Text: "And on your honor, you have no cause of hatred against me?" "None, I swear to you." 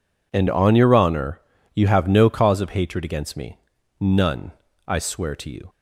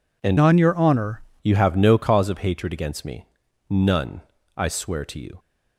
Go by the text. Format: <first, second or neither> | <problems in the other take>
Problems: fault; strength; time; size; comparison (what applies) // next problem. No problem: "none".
first | changes voice from "on" to "honor"; from 0.3 to 1.2 s; 0.9 s long